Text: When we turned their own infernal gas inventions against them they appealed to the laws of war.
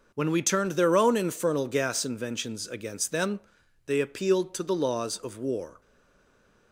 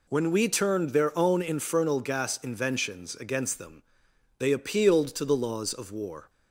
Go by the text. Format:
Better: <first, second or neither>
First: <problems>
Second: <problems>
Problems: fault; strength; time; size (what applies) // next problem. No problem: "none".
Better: second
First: pauses between "them" and "they"; noticeable; at 3.3 s; 0.48 s long // stays silent after the last word; slight; from 5.8 s on; 0.9 s long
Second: pauses between "them" and "they"; noticeable; at 3.8 s; 0.56 s long